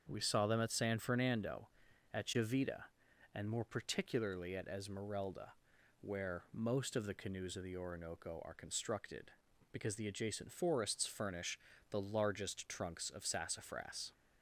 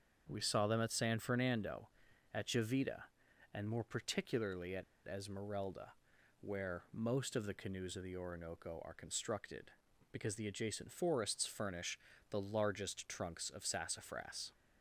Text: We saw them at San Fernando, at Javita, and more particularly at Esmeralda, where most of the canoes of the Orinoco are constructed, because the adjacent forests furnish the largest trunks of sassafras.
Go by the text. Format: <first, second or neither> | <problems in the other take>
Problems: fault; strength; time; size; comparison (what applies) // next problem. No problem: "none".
first | starts louder than the rest; strong; until 1.2 s; 7 dB; strong in the first // pauses between "at" and "Esmeralda"; slight; at 4.8 s; 0.21 s long // pauses between "furnish" and "the"; slight; at 11.9 s; 0.32 s long; slight in the first